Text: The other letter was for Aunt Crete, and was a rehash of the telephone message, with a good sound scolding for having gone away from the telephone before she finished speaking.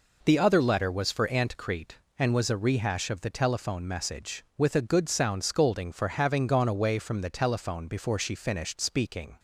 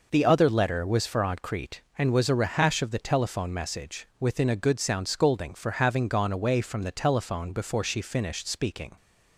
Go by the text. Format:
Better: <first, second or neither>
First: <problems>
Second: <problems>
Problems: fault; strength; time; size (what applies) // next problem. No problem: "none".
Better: first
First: none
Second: says "within" for "with"; at 4.1 s